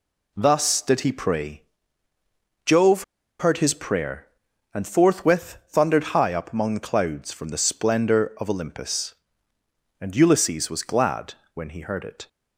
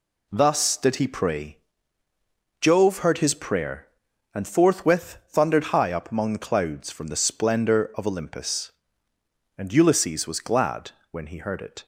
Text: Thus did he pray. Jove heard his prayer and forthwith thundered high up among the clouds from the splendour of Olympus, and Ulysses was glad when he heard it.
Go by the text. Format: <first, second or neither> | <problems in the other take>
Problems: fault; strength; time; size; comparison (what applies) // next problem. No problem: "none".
second | pauses between "Jove" and "heard"; at 3.0 s; 0.36 s long // pauses between "glad" and "when"; slight; at 11.3 s; 0.20 s long; slight in the second